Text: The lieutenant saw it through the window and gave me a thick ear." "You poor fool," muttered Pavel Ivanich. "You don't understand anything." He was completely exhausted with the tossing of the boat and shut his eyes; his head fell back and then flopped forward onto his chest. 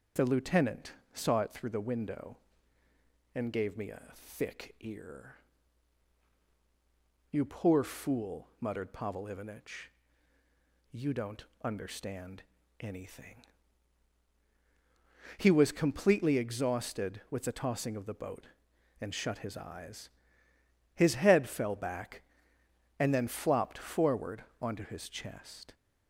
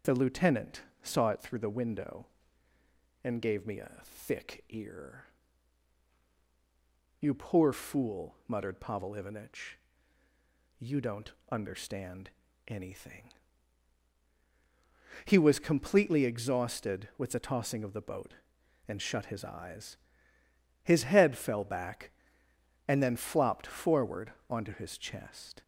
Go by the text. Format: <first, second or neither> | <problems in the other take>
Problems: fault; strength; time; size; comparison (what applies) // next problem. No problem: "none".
neither | starts louder than the rest; the same in both // pauses between "lieutenant" and "saw"; slight; the same in both // pauses between "don't" and "understand"; slight; the same in both // pauses between "understand" and "anything"; the same in both // pauses between "forward" and "onto"; slight; the same in both